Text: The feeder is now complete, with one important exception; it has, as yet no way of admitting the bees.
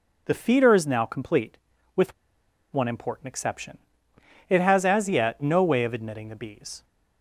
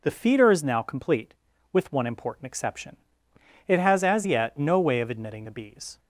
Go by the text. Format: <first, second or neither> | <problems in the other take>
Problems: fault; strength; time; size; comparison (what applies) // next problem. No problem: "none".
second | pauses between "with" and "one"; noticeable; at 2.1 s; 0.58 s long